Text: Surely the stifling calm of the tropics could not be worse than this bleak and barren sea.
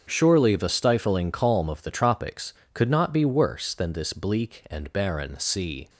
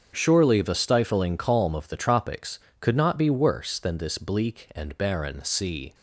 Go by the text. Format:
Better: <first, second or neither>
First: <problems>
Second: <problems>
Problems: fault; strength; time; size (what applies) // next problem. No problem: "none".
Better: neither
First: starts louder than the rest; strong; until 1.0 s; 7 dB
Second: starts louder than the rest; strong; until 1.1 s; 7 dB